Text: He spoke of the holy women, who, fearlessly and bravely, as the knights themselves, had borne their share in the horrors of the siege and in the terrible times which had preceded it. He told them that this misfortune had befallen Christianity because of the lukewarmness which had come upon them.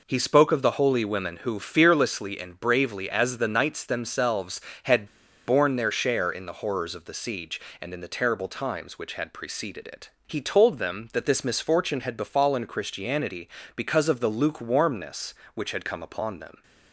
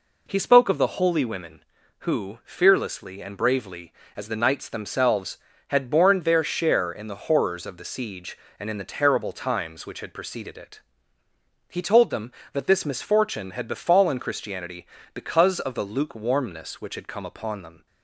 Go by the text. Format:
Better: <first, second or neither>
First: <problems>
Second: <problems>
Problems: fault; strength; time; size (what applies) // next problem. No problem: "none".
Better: second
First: pauses between "had" and "borne"; at 5.0 s; 0.40 s long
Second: none